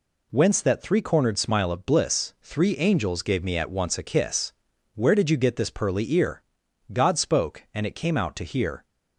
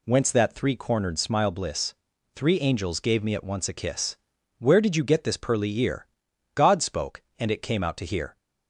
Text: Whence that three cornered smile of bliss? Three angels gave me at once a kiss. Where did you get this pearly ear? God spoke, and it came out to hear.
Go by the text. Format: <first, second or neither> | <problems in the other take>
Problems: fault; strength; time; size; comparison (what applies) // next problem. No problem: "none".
first | skips "of"; at 1.5 s